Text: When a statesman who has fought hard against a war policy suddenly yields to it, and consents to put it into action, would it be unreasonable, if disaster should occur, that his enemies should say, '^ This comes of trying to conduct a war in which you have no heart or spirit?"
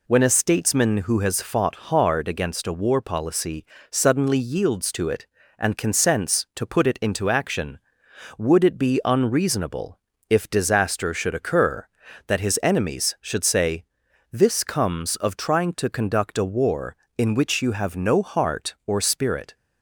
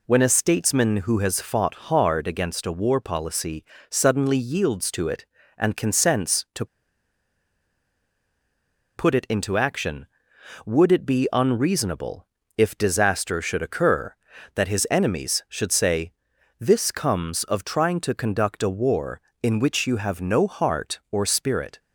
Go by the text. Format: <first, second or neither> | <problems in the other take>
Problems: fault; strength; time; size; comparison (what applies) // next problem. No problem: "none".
first | pauses between "fought" and "hard"; slight; at 1.7 s; 0.16 s long; slight in the first // pauses between "policy" and "suddenly"; slight; at 3.6 s; 0.26 s long; slight in the first // pauses between "to" and "put"; strong; at 6.6 s; 2.3 s long